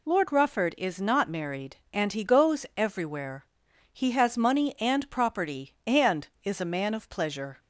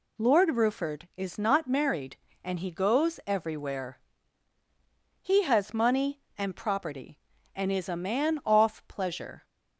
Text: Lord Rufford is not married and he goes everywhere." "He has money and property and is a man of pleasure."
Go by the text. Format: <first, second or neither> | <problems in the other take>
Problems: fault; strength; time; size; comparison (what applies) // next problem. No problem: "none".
first | says "off" for "of"; at 8.4 s